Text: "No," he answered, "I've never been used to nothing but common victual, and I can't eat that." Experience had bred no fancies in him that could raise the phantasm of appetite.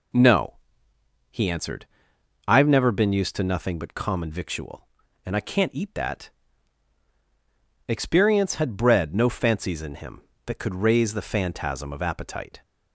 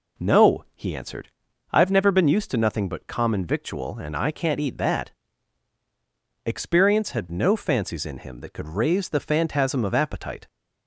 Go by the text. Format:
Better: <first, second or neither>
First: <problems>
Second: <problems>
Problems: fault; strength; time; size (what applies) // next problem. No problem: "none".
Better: first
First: none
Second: skips "bred"; at 7.2 s